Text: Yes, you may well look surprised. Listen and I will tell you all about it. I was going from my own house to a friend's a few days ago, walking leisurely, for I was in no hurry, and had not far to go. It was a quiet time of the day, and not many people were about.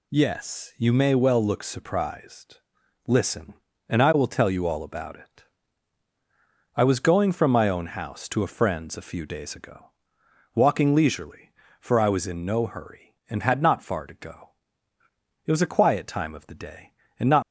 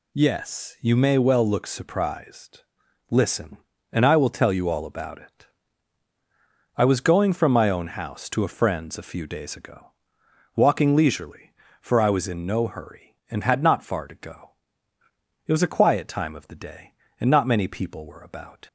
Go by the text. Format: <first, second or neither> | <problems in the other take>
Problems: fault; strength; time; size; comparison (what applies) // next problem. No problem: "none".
second | stops before "many people were about"; at 17.4 s